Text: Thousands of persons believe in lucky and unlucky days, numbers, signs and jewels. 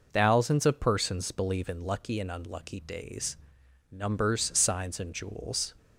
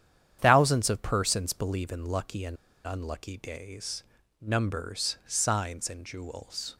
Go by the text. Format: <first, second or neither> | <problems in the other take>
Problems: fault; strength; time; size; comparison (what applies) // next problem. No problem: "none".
first | starts louder than the rest; strong; until 1.4 s; 9.5 dB // pauses between "and" and "unlucky"; slight; at 2.5 s; 0.30 s long